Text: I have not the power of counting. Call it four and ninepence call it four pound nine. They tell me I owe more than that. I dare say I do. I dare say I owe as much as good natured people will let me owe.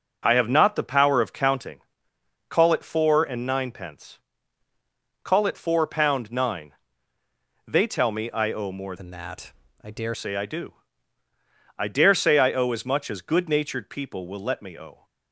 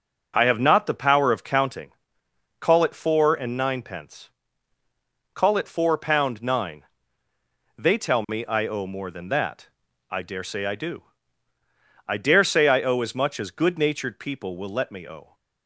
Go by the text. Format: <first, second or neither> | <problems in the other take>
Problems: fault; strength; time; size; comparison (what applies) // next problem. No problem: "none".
second | pauses between "ninepence" and "call"; at 4.1 s; 1.0 s long; also in the second // changes voice from "than" to "dare"; from 8.9 to 10.1 s; 1.2 s long